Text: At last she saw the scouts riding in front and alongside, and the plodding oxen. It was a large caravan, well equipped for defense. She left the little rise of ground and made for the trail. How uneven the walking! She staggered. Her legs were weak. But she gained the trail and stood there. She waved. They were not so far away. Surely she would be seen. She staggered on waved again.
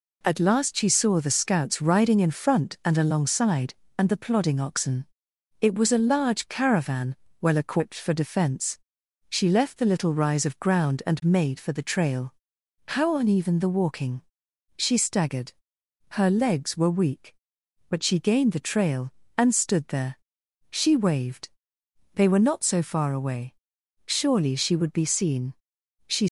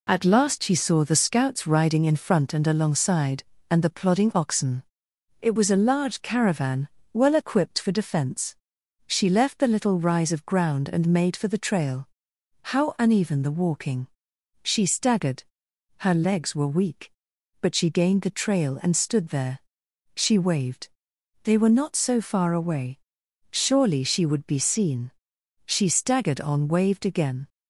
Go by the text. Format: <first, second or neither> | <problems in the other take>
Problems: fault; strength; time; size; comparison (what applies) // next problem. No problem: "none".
second | stops before "staggered on waved again"; at 26.2 s